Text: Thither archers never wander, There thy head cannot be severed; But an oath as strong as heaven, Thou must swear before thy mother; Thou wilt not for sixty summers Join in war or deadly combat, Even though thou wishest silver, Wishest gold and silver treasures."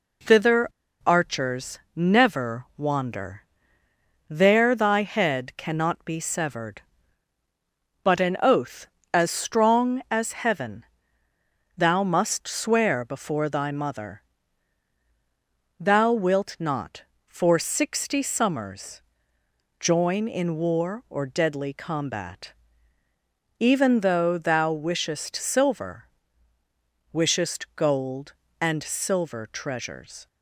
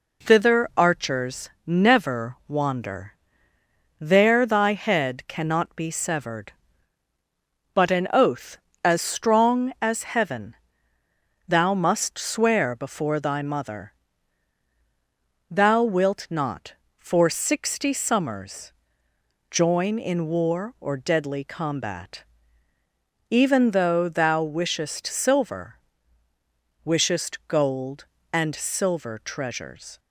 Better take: second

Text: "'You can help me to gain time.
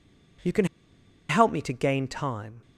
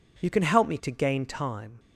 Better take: second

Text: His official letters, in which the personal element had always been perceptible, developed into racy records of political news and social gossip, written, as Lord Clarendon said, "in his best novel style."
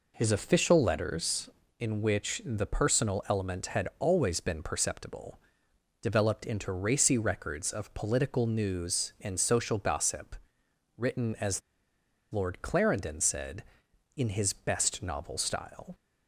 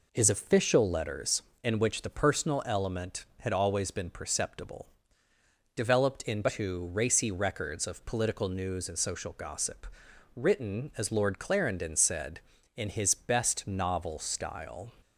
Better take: second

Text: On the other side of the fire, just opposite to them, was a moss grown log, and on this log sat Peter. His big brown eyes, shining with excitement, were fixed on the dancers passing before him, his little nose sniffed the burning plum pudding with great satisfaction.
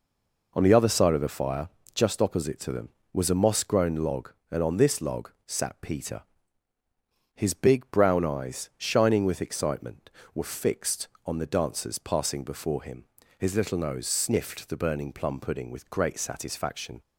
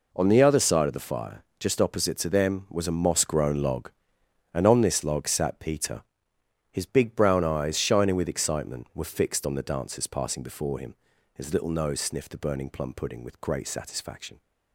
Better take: second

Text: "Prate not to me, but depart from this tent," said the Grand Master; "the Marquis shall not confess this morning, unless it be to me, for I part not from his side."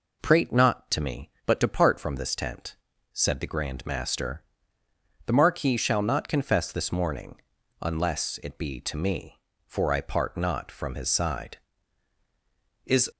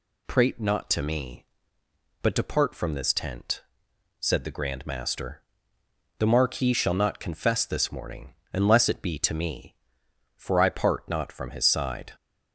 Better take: second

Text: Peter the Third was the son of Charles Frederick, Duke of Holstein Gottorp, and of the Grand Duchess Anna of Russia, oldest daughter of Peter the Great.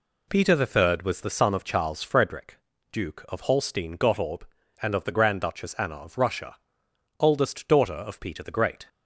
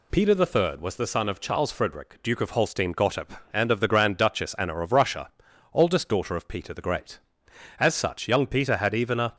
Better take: first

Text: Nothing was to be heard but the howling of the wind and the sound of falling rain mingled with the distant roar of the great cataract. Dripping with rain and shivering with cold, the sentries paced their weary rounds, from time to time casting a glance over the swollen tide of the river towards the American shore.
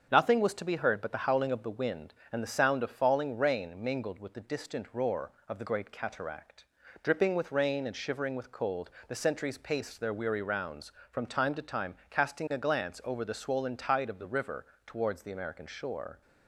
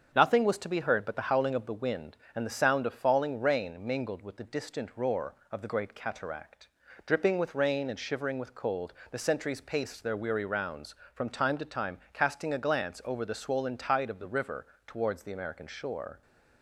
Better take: neither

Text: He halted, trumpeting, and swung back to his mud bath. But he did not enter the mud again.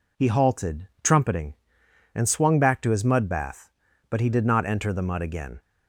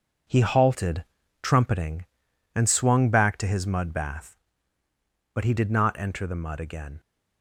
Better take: first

